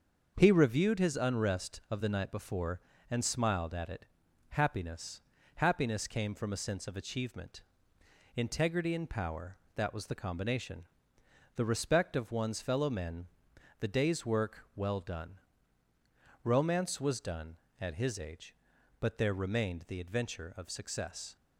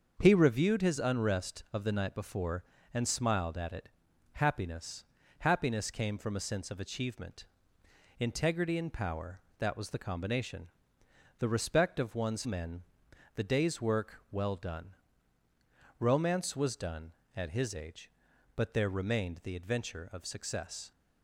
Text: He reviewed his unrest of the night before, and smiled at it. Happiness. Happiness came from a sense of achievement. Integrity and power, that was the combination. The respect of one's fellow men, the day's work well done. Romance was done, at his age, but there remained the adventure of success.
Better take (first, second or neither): first